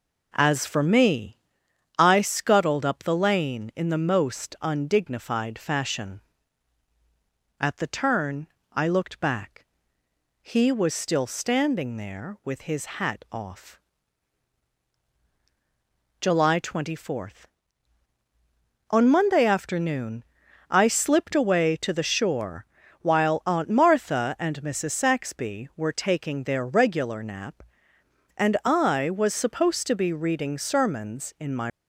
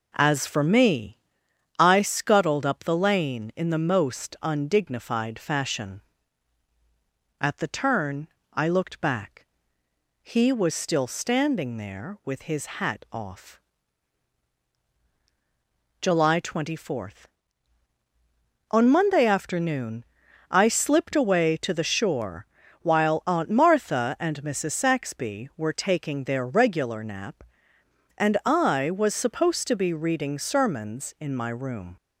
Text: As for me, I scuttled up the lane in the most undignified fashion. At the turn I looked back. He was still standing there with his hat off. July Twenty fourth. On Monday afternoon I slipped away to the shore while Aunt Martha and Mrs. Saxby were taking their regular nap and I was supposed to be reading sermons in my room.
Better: second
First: pauses between "turn" and "I"; slight; at 8.4 s; 0.24 s long // pauses between "afternoon" and "I"; noticeable; at 20.2 s; 0.46 s long // pauses between "shore" and "while"; slight; at 22.6 s; 0.36 s long // stops before "room"; at 31.6 s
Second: pauses between "turn" and "I"; slight; at 8.2 s; 0.24 s long // pauses between "afternoon" and "I"; noticeable; at 20.0 s; 0.46 s long // pauses between "shore" and "while"; slight; at 22.4 s; 0.36 s long

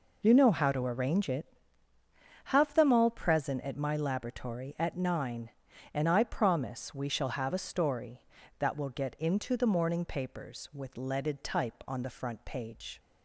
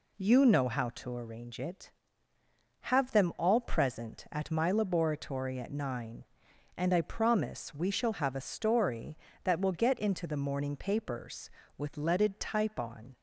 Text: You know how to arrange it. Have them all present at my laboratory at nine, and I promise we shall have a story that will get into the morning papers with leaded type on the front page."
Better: first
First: none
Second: stops before "the front page"; at 13.1 s

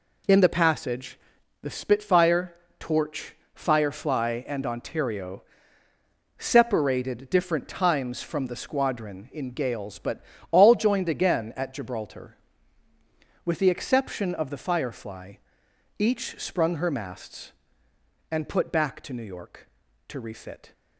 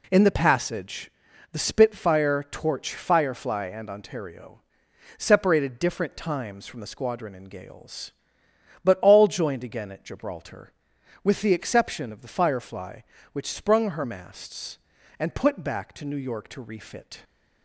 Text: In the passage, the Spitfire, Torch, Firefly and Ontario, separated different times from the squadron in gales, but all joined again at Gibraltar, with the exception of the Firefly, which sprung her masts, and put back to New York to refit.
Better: second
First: pauses between "but" and "all"; slight; at 10.2 s; 0.28 s long // says "each" for "which"; at 15.9 s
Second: none

